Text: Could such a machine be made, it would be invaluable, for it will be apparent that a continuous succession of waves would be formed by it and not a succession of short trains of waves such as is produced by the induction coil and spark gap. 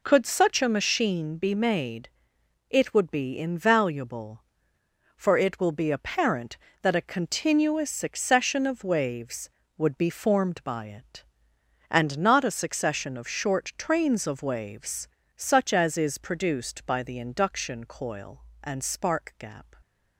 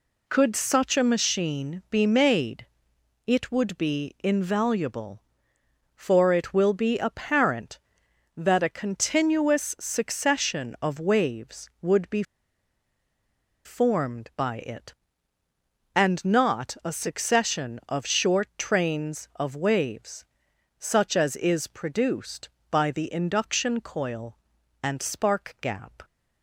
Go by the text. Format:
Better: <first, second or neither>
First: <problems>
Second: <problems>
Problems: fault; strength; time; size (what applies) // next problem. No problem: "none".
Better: first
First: pauses between "waves" and "such"; slight; at 15.0 s; 0.30 s long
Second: pauses between "be" and "formed"; strong; at 12.2 s; 1.4 s long // pauses between "waves" and "such"; noticeable; at 20.2 s; 0.54 s long